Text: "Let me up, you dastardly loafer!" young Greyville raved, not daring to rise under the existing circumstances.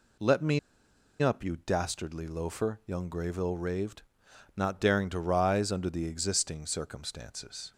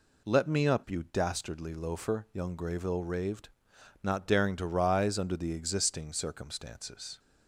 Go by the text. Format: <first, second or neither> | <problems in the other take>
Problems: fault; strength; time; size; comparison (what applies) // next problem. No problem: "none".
second | pauses between "me" and "up"; noticeable; at 0.5 s; 0.62 s long